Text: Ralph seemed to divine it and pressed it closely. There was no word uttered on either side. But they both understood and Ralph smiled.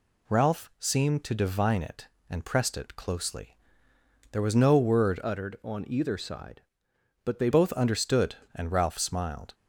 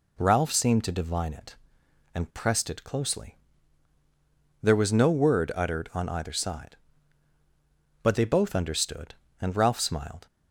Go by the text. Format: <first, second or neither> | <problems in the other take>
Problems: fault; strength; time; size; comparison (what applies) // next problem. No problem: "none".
second | changes voice from "uttered" to "they"; from 5.2 to 7.4 s; 2.2 s long